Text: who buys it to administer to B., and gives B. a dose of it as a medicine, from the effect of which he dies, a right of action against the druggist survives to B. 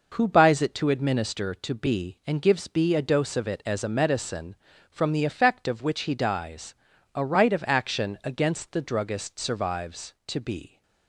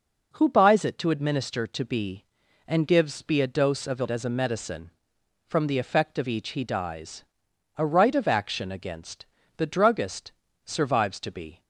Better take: first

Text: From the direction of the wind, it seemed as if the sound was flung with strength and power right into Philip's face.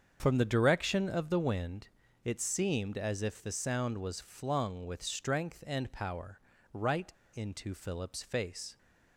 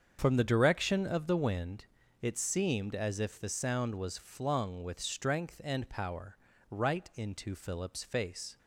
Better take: second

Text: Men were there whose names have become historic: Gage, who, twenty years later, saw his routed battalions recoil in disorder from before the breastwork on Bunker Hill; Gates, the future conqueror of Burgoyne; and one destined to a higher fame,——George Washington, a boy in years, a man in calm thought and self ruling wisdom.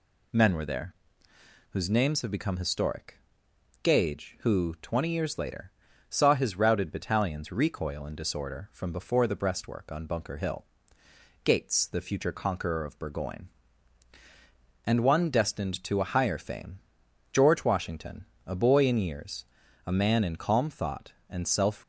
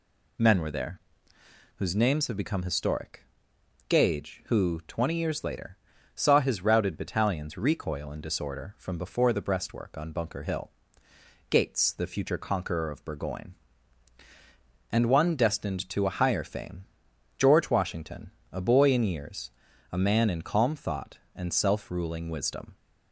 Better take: second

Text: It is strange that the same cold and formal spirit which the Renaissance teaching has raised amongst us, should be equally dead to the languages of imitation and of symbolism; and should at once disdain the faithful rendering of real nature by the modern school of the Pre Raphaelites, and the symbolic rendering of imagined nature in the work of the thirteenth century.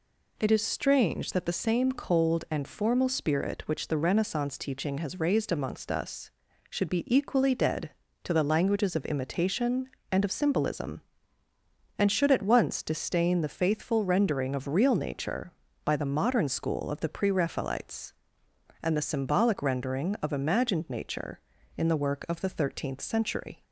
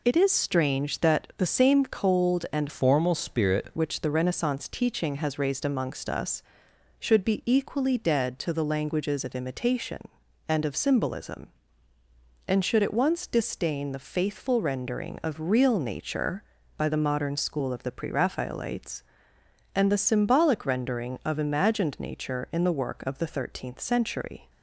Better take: first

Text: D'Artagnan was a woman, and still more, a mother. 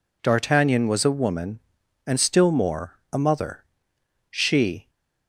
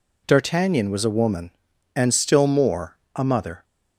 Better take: second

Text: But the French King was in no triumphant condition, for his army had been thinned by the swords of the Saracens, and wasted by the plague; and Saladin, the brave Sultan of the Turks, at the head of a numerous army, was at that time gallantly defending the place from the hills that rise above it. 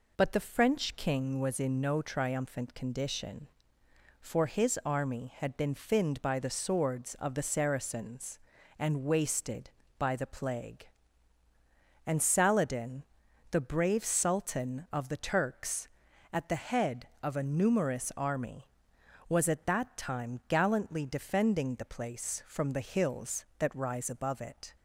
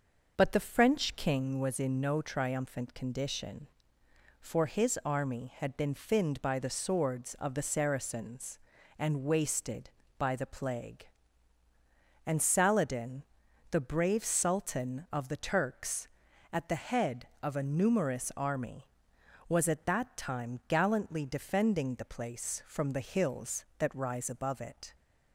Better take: first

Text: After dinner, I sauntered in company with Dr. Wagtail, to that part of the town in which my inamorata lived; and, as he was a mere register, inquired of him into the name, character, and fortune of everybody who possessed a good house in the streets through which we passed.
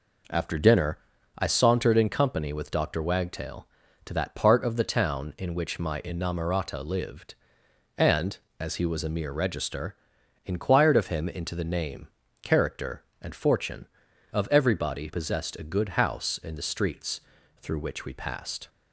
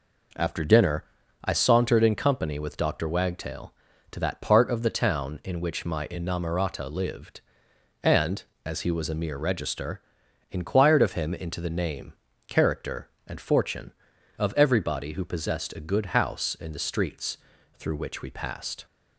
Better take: second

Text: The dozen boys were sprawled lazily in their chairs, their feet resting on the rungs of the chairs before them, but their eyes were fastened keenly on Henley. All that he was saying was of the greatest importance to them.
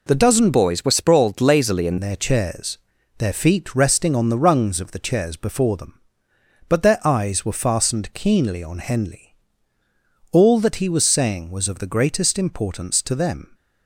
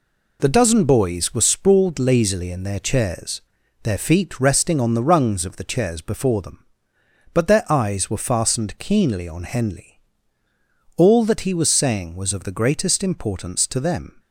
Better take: second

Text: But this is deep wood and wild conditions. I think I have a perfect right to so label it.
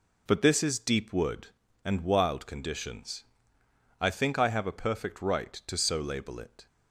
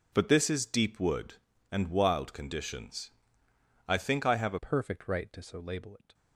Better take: first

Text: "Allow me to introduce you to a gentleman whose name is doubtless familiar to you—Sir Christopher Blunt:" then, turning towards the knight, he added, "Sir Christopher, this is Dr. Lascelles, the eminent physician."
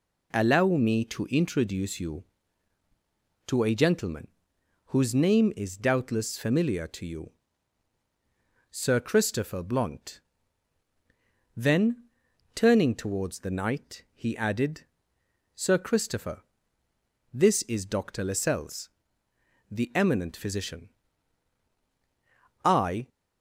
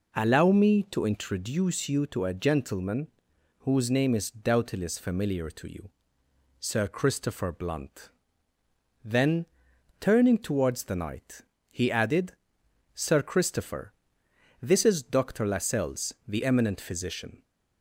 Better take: second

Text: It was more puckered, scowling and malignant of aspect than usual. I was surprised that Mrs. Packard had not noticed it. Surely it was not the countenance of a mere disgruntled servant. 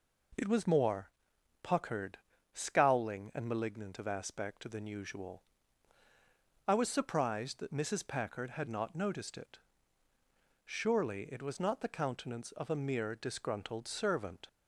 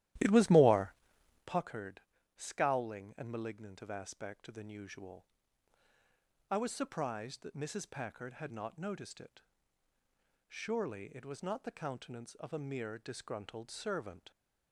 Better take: first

